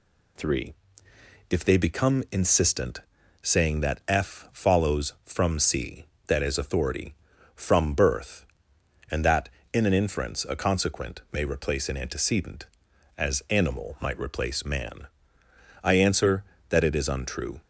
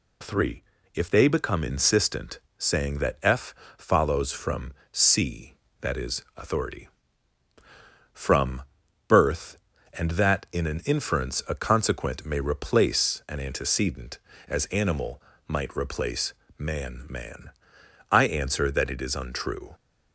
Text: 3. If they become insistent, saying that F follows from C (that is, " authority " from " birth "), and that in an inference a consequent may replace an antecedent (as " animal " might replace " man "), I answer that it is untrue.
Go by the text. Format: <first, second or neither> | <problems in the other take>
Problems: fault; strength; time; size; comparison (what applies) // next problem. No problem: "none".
first | pauses between "F" and "follows"; slight; at 3.5 s; 0.22 s long // pauses between "from" and "C"; slight; at 4.7 s; 0.20 s long // says "man" twice; at 17.0 s